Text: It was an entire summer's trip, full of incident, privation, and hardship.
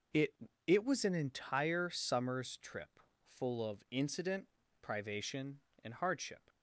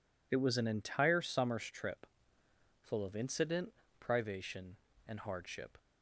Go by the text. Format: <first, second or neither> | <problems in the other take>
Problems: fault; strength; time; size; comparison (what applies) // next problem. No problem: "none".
second | says "It" twice; at 0.6 s